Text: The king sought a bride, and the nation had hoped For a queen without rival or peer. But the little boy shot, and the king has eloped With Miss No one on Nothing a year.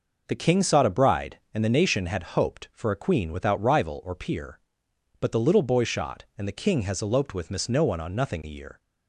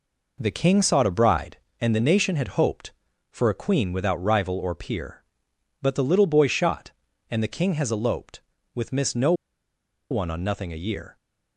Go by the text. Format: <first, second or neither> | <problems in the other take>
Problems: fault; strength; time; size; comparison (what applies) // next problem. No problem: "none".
first | pauses between "No" and "one"; noticeable; at 9.3 s; 0.77 s long